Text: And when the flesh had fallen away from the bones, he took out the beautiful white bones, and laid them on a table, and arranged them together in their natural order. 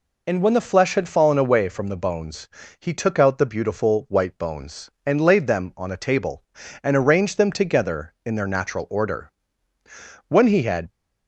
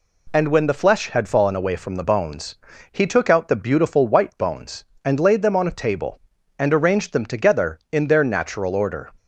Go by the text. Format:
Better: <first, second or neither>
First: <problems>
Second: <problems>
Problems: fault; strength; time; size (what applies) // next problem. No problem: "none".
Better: second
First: goes on to say "When he had"; noticeable; from 10.2 s on; 0.62 s long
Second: none